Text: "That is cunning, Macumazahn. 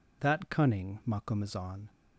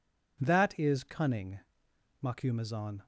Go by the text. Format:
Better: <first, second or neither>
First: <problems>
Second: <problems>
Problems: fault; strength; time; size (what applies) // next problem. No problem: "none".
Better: second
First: skips "is"; at 0.4 s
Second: none